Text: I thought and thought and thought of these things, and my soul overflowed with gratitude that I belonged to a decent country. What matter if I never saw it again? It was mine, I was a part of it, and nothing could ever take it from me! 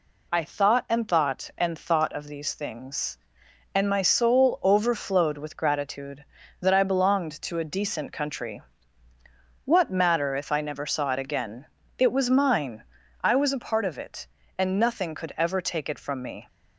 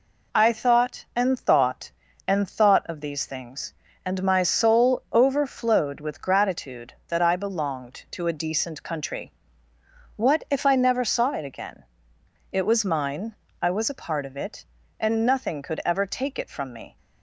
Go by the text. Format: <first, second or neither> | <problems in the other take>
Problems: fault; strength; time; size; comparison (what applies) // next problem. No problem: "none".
first | skips "matter"; at 10.4 s